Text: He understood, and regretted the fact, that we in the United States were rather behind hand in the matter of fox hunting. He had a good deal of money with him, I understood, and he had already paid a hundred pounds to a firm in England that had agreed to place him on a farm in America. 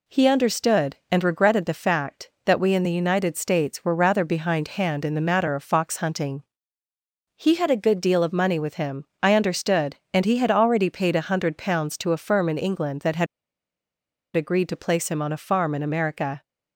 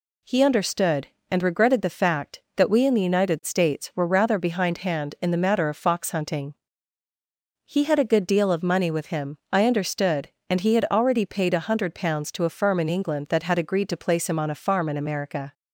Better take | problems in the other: second | pauses between "had" and "agreed"; at 13.2 s; 1.1 s long

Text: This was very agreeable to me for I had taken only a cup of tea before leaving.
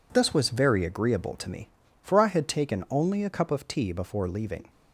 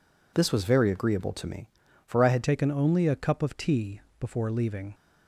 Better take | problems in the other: first | changes voice at "taken"; from 2.4 s on; 2.5 s long // pauses between "tea" and "before"; slight; at 4.0 s; 0.18 s long

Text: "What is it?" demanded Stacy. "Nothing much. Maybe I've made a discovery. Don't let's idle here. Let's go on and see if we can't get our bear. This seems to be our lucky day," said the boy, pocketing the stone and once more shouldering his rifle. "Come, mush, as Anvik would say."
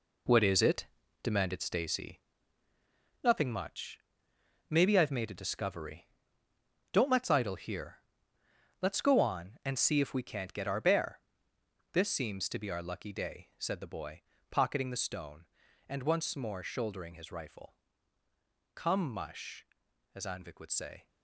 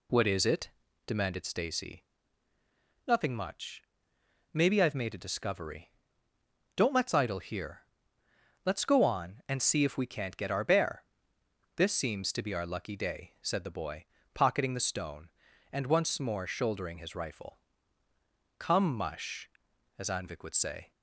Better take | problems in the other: second | gets quieter; strong; throughout; 8 dB

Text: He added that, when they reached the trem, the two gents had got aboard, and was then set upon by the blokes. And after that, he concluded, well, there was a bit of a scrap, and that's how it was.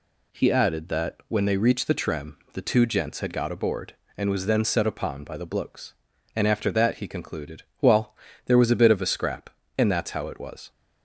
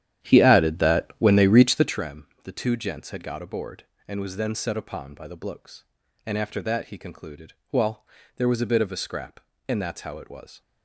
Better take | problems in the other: first | starts louder than the rest; strong; until 2.1 s; 10.5 dB

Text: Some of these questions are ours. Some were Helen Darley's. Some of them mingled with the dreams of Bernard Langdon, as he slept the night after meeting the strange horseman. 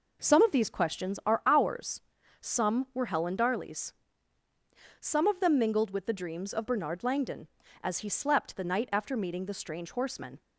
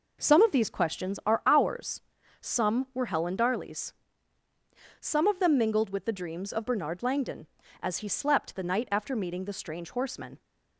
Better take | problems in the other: neither | none

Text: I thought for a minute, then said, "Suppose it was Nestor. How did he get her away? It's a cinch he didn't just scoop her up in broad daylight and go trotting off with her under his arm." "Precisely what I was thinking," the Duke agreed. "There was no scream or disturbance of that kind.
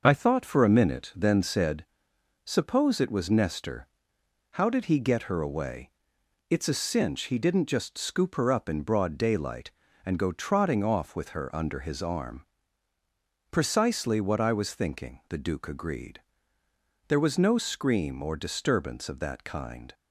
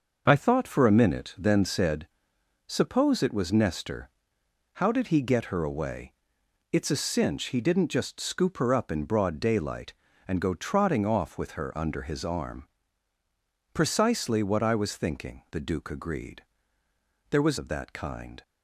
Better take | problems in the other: first | skips "no scream or disturbance"; at 17.5 s

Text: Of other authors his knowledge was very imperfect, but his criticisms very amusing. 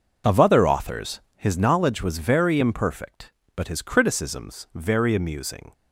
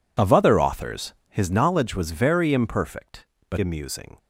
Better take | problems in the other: first | skips "his criticisms very"; at 3.5 s

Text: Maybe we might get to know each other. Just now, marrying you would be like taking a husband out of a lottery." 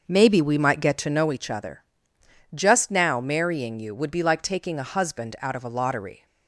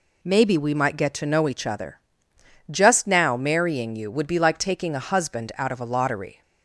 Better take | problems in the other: second | starts louder than the rest; noticeable; until 1.2 s; 6 dB

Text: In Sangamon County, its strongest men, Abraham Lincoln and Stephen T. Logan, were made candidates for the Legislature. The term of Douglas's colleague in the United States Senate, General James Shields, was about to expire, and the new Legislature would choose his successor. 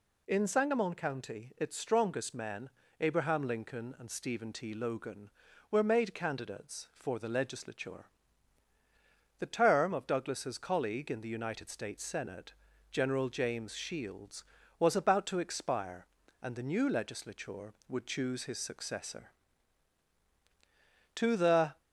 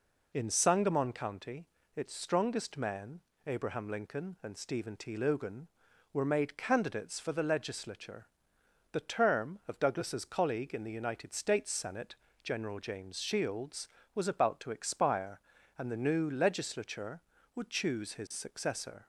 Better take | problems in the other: second | goes on to say "To the"; noticeable; from 21.1 s on; 0.64 s long

